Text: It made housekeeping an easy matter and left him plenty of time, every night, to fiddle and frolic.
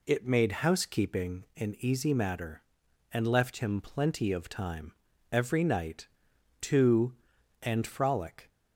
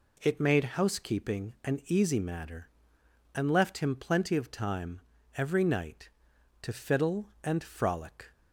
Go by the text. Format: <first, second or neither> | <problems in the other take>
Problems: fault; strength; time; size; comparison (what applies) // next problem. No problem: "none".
second | skips "fiddle"; at 7.3 s